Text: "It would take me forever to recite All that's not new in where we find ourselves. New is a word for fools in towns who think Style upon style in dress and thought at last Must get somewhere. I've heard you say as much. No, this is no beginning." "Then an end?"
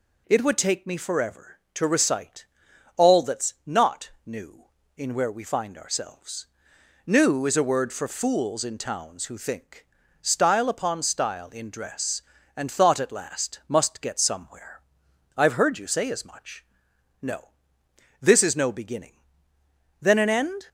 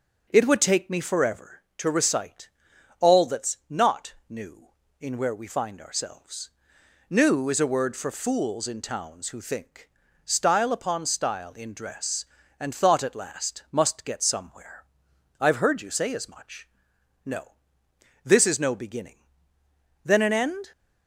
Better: first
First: pauses between "recite" and "All"; noticeable; at 2.4 s; 0.50 s long // pauses between "think" and "Style"; slight; at 9.8 s; 0.36 s long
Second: starts louder than the rest; until 1.6 s; 6.5 dB // pauses between "recite" and "All"; noticeable; at 2.4 s; 0.50 s long // pauses between "think" and "Style"; slight; at 9.8 s; 0.36 s long

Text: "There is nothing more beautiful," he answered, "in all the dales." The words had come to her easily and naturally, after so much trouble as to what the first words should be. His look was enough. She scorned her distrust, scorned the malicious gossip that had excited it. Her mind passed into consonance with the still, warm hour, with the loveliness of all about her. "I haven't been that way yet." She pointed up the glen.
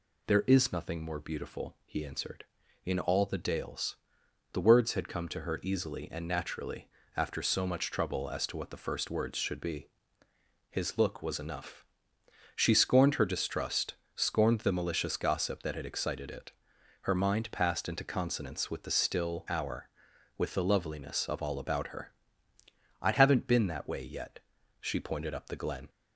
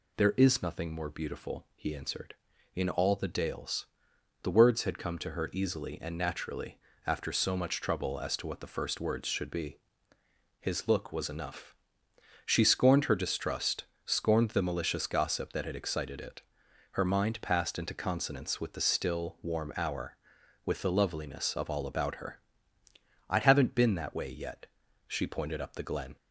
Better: second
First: skips "warm"; at 19.4 s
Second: none

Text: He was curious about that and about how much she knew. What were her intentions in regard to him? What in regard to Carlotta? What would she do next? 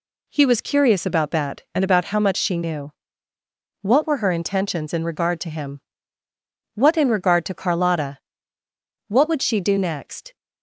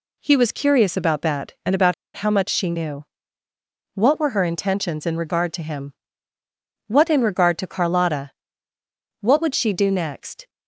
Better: first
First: none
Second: pauses between "about" and "how"; slight; at 1.9 s; 0.22 s long

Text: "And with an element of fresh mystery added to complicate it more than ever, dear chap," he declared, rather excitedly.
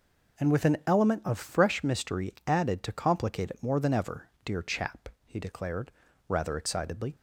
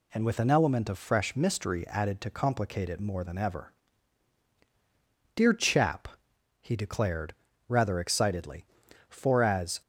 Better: first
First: none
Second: goes on to say "For as"; noticeable; from 9.0 s on; 0.72 s long

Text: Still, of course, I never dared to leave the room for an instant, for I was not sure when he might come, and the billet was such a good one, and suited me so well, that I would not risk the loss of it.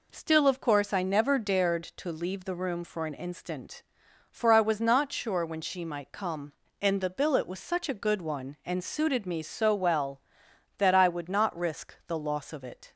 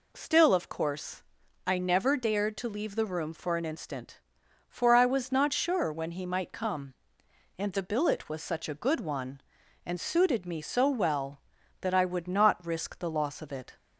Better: second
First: says "she" for "he"; at 5.6 s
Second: none

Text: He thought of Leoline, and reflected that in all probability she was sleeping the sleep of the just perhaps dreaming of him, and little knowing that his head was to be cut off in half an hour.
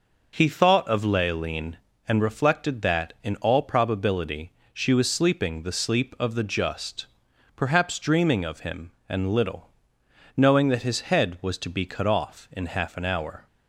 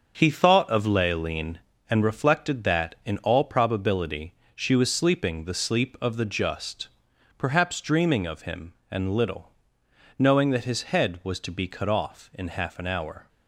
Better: first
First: pauses between "probability" and "she"; slight; at 4.5 s; 0.22 s long // pauses between "just" and "perhaps"; noticeable; at 7.0 s; 0.48 s long // pauses between "little" and "knowing"; noticeable; at 9.7 s; 0.66 s long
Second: gets quieter; strong; throughout; 7.5 dB // pauses between "probability" and "she"; slight; at 4.3 s; 0.22 s long // pauses between "just" and "perhaps"; noticeable; at 6.8 s; 0.48 s long // pauses between "little" and "knowing"; noticeable; at 9.5 s; 0.66 s long

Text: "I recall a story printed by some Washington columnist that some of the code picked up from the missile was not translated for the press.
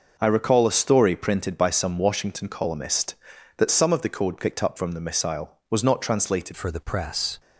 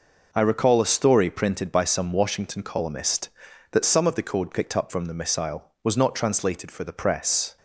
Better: second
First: changes voice at "for"; from 6.5 s on; 0.8 s long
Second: none

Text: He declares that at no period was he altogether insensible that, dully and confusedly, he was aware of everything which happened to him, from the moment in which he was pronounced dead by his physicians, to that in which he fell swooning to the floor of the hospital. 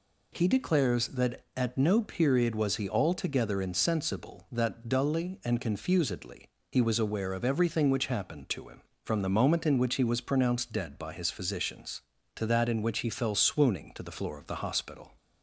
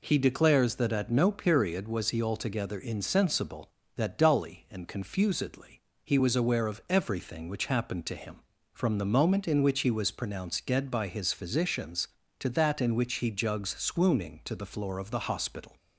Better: first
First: none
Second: says "jugs" for "fell"; at 13.2 s

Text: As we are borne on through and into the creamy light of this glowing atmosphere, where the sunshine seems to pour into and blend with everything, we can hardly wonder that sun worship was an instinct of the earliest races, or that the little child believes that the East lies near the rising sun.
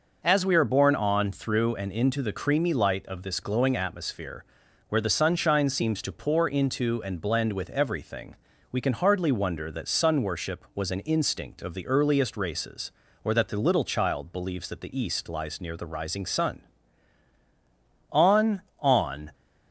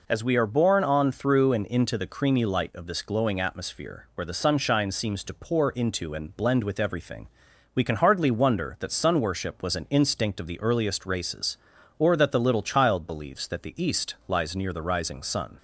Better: second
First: goes on to say "On on"; noticeable; from 18.1 s on; 1.2 s long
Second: none

